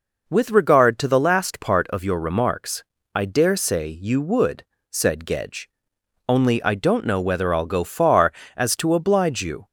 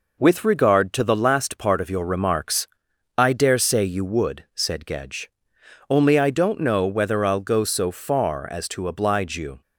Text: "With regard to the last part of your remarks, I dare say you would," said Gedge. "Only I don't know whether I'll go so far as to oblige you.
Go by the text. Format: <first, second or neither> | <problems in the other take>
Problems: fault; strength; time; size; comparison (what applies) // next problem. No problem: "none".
second | skips "so"; at 7.8 s